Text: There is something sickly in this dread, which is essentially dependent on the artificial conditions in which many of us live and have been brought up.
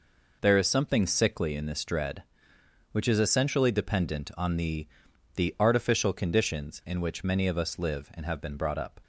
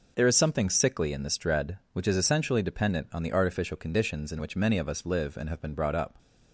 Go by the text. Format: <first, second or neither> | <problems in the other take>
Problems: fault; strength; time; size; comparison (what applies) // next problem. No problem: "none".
second | says "the" twice; at 5.3 s